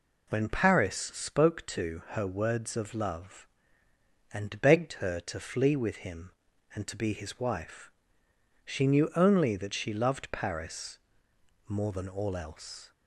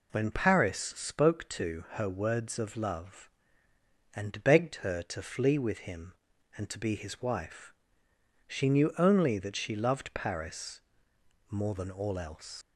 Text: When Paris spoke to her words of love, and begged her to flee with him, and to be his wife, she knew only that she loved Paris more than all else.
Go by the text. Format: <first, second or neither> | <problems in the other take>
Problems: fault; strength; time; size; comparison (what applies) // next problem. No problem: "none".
first | pauses between "Paris" and "more"; noticeable; at 10.7 s; 0.68 s long; noticeable in the first // leaves "else" unfinished; at 12.6 s; 125 ms